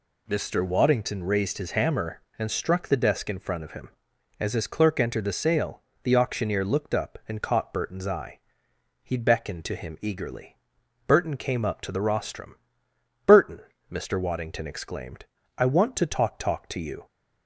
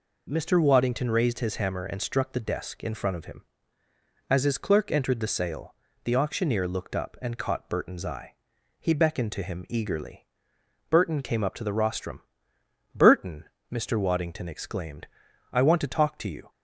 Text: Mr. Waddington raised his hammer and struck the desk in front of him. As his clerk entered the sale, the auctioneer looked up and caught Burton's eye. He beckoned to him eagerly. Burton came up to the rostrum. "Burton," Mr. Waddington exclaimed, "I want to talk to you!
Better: second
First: says "talk" twice; at 16.3 s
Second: none

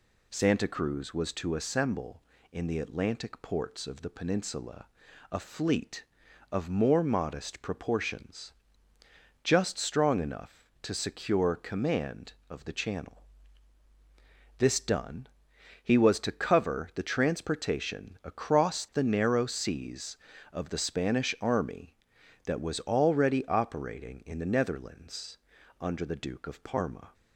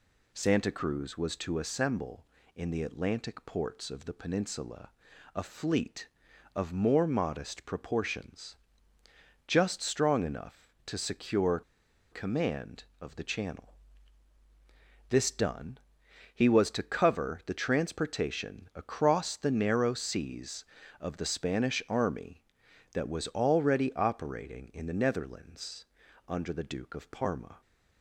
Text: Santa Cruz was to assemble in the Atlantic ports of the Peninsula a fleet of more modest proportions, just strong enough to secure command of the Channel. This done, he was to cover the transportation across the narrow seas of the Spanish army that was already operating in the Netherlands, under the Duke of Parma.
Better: first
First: pauses between "Peninsula" and "a"; noticeable; at 4.8 s; 0.46 s long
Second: pauses between "Peninsula" and "a"; noticeable; at 4.8 s; 0.46 s long // pauses between "secure" and "command"; noticeable; at 11.6 s; 0.48 s long

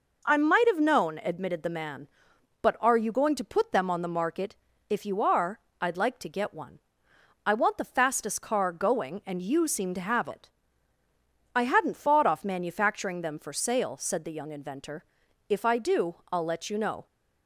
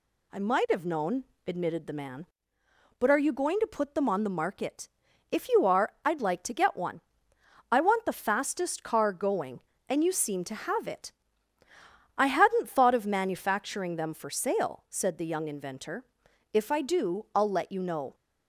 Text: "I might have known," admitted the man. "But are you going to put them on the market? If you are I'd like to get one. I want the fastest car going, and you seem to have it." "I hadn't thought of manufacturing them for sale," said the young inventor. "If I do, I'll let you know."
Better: second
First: pauses between "are" and "I'd"; slight; at 5.5 s; 0.22 s long // says "off" for "of"; at 12.2 s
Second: none

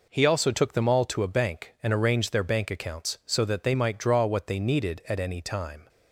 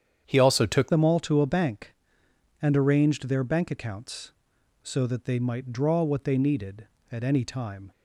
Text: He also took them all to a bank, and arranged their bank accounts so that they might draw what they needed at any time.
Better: first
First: none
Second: starts louder than the rest; strong; until 1.2 s; 8.5 dB // changes voice at "them"; from 0.8 s on; 7.1 s long

